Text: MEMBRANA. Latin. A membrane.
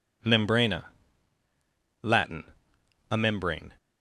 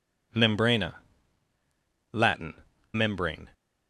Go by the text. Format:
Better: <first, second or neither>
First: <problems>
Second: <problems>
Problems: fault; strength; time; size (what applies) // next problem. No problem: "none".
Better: first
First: none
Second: skips "A"; at 2.7 s